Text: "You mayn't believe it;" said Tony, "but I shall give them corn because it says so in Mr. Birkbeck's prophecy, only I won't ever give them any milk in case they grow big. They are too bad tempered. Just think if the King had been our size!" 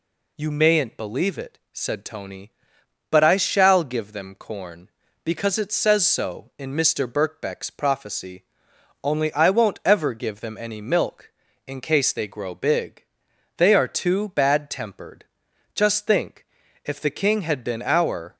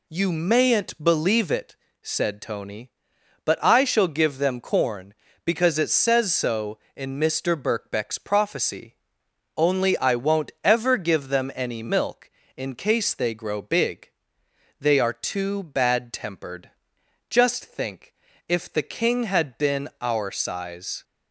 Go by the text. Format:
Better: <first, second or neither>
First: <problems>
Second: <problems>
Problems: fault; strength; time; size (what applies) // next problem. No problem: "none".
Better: second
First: pauses between "think" and "if"; at 16.4 s; 0.40 s long // stops before "size"; at 18.3 s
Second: pauses between "think" and "if"; slight; at 18.1 s; 0.34 s long